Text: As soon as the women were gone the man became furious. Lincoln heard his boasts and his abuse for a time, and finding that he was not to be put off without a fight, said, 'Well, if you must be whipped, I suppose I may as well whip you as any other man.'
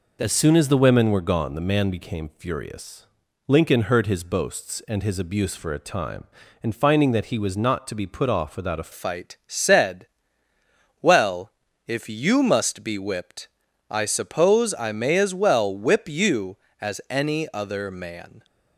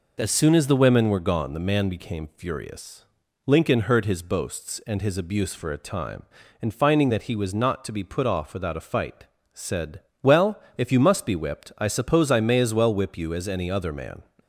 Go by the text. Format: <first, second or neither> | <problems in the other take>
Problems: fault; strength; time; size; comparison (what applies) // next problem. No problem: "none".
second | changes voice at "fight"; from 8.9 s on; 9.5 s long